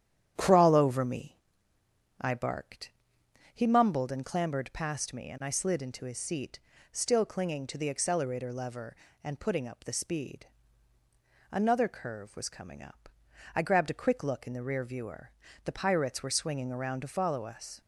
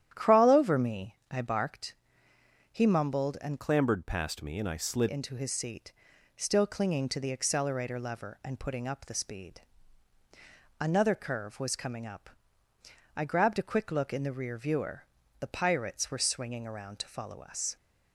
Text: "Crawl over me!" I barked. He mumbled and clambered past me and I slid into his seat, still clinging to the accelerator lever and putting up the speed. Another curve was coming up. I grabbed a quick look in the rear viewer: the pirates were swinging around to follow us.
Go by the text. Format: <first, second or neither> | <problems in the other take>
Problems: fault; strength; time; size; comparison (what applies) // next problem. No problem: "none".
first | starts louder than the rest; strong; until 1.1 s; 10.5 dB; strong in the first // changes voice from "clambered" to "slid"; from 3.5 to 5.0 s; 1.5 s long